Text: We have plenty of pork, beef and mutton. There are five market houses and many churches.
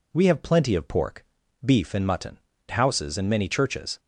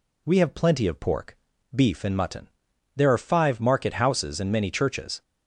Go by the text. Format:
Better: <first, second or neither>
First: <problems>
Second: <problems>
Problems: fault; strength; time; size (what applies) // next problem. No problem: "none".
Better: second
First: skips "There are five market"; at 2.5 s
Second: none